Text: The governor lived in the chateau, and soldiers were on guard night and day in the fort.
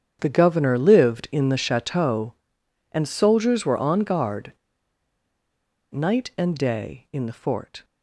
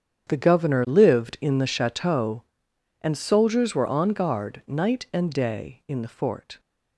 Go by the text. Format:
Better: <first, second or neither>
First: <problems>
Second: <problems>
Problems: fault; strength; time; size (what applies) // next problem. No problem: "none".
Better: second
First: starts louder than the rest; strong; until 1.2 s; 8.5 dB // pauses between "guard" and "night"; strong; at 4.5 s; 1.4 s long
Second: starts louder than the rest; strong; until 1.3 s; 8.5 dB